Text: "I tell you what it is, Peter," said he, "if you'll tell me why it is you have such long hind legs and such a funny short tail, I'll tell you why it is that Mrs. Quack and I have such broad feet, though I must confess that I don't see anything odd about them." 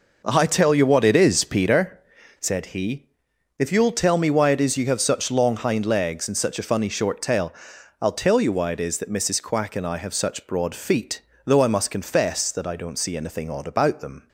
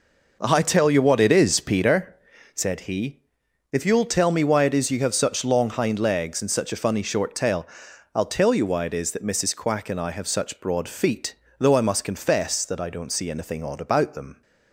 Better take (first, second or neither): neither